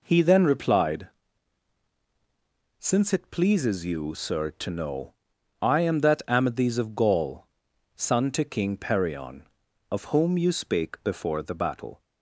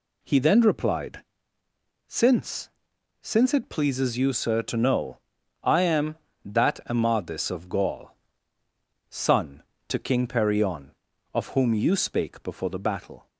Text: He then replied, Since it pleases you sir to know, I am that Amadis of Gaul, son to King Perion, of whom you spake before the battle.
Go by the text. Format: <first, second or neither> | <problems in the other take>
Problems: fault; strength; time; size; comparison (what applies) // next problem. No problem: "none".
first | says "Since" twice; at 3.2 s